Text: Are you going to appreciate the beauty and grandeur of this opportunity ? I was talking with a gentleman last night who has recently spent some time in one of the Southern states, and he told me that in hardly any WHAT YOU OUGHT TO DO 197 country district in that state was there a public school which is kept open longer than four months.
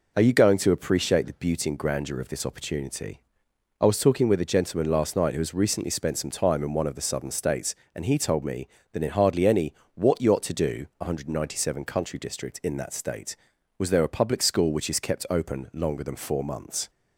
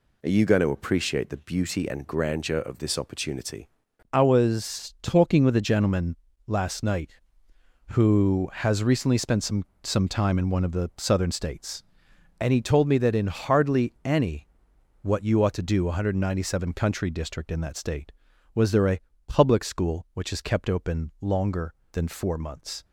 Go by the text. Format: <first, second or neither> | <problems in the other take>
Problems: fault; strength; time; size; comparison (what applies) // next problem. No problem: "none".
first | pauses between "gentleman" and "last"; slight; at 6.1 s; 0.32 s long // says "some" twice; at 9.8 s // pauses between "any" and "WHAT"; noticeable; at 14.4 s; 0.56 s long; slight in the first // pauses between "a" and "public"; slight; at 19.0 s; 0.26 s long